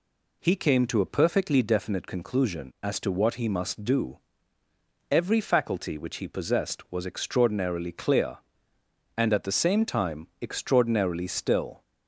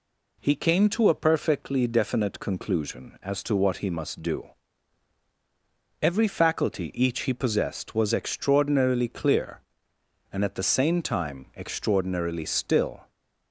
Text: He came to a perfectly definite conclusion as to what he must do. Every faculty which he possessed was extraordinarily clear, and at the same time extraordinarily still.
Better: first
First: none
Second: says "each" for "which"; at 6.9 s

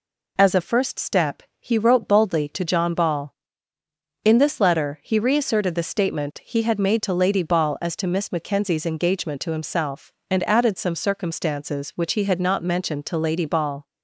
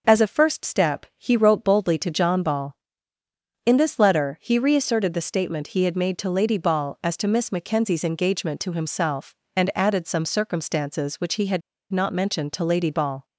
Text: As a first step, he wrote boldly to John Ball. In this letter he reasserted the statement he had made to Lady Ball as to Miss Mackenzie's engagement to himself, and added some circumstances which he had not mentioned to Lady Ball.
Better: first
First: none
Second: pauses between "had" and "not"; slight; at 11.6 s; 0.31 s long

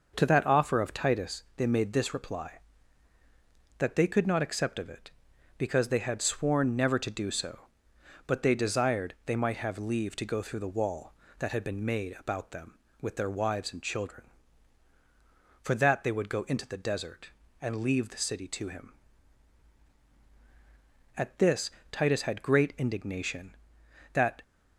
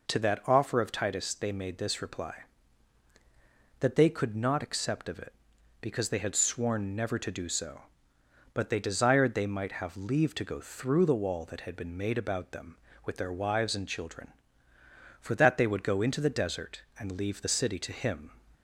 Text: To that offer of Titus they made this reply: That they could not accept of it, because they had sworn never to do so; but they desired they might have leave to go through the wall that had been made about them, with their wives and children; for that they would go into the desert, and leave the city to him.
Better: second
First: goes on to say "At this Titus had great indignation that"; strong; from 21.1 s on; 3.2 s long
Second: none

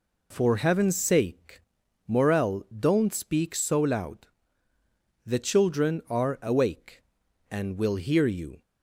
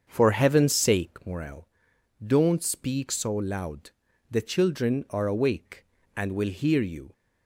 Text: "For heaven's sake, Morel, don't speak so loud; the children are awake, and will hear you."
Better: first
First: none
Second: starts louder than the rest; until 1.3 s; 7 dB

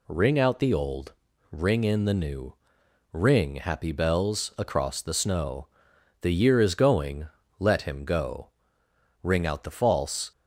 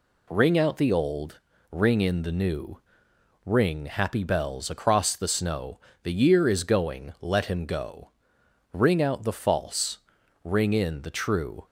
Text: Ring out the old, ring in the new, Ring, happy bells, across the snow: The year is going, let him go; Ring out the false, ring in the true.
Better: second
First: stops before "ring in the true"; at 10.3 s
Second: none

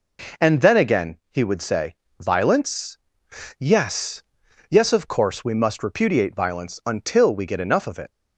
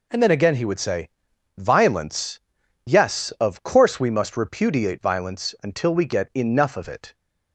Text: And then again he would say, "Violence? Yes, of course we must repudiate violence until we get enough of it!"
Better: second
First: says "Yes" twice; at 4.6 s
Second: none

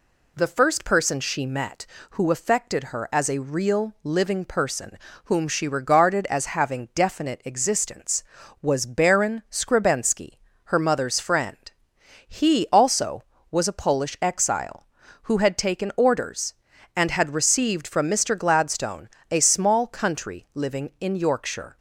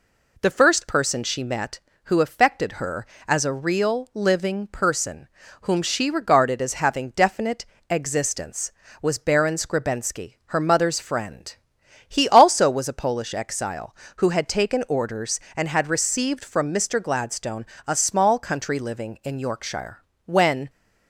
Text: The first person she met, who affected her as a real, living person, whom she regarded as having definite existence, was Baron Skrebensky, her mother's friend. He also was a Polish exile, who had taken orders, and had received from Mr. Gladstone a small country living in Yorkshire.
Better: first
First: pauses between "Gladstone" and "a"; slight; at 19.0 s; 0.24 s long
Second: pauses between "definite" and "existence"; slight; at 7.6 s; 0.24 s long // pauses between "Gladstone" and "a"; slight; at 17.6 s; 0.20 s long // goes on to say "When"; slight; from 20.2 s on; 0.44 s long

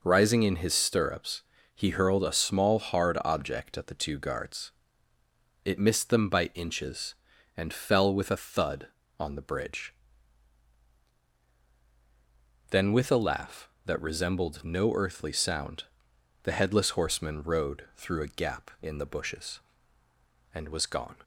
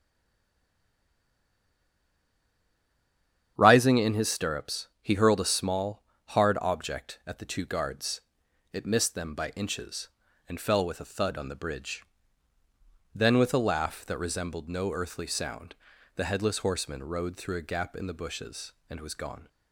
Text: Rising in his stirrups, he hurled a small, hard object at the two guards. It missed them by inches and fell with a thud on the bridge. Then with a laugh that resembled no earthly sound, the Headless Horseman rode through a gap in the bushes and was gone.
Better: first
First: none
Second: stays silent before the first word; strong; until 3.5 s; 3.5 s long // starts louder than the rest; strong; until 4.5 s; 9 dB

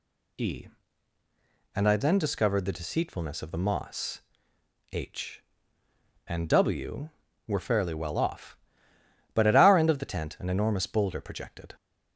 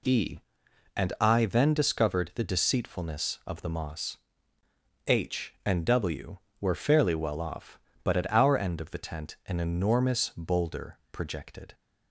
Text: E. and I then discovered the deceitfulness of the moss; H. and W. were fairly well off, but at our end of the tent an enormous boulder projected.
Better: neither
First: none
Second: none

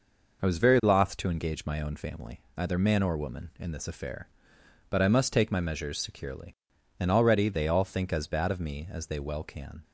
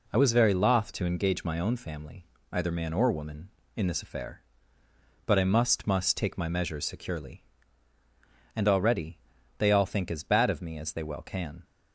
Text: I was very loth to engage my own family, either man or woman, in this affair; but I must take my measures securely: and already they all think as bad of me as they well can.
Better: first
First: none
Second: says "must" twice; at 5.8 s // pauses between "already" and "they"; at 9.1 s; 0.40 s long

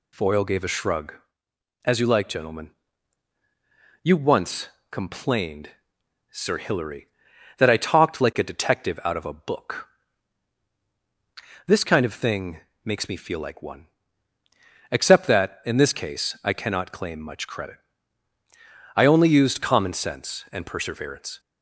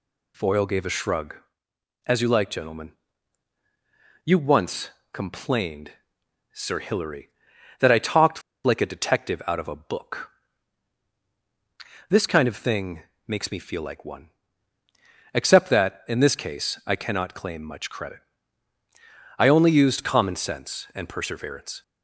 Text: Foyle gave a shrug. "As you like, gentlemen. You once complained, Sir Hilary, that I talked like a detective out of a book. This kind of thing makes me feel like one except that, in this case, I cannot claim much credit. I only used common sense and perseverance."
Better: first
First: pauses between "once" and "complained"; slight; at 4.6 s; 0.24 s long // pauses between "thing" and "makes"; slight; at 12.5 s; 0.22 s long // pauses between "one" and "except"; at 13.8 s; 1.0 s long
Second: pauses between "once" and "complained"; slight; at 4.8 s; 0.24 s long // pauses between "talked" and "like"; slight; at 8.4 s; 0.22 s long // pauses between "thing" and "makes"; slight; at 13.0 s; 0.22 s long // pauses between "one" and "except"; at 14.3 s; 1.0 s long

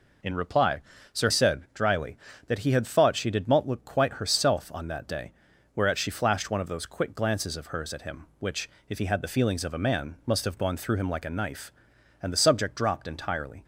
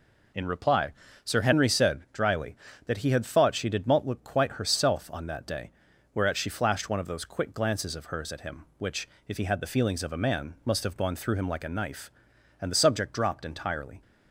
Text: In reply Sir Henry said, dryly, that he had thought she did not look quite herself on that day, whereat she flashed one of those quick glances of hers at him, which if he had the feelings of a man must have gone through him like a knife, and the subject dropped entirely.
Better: second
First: pauses between "reply" and "Sir"; slight; at 0.8 s; 0.32 s long // skips "Henry"; at 1.2 s // pauses between "which" and "if"; slight; at 8.6 s; 0.18 s long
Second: pauses between "reply" and "Sir"; slight; at 0.9 s; 0.32 s long // pauses between "which" and "if"; slight; at 9.0 s; 0.18 s long

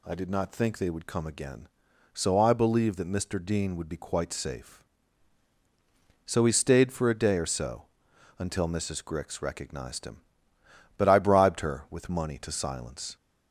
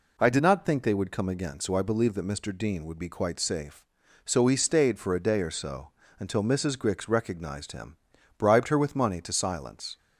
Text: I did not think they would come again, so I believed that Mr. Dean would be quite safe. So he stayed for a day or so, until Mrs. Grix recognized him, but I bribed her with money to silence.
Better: first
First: none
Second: skips "but I"; at 8.1 s

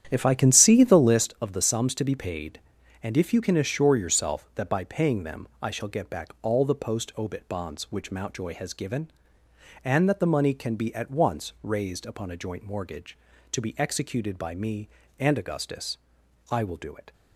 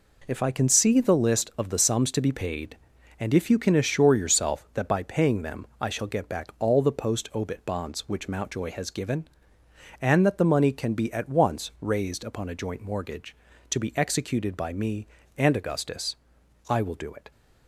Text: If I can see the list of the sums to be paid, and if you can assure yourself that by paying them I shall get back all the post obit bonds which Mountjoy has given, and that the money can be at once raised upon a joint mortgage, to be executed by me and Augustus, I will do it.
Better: second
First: starts louder than the rest; strong; until 1.3 s; 10 dB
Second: none

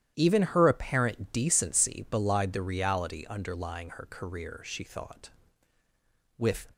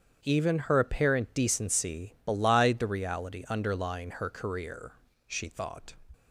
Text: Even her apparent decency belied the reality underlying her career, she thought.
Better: second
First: starts louder than the rest; strong; until 1.1 s; 11.5 dB // goes on to say "With"; slight; from 6.3 s on; 0.34 s long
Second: starts louder than the rest; strong; until 1.2 s; 8 dB

